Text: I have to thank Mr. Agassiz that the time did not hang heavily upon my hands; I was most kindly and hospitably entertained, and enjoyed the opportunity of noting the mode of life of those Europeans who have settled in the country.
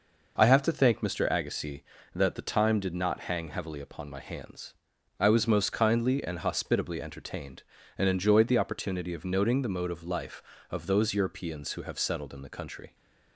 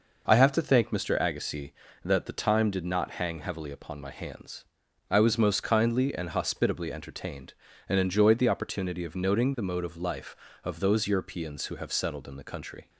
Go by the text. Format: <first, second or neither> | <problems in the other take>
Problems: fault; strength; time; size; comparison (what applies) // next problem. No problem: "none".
neither | none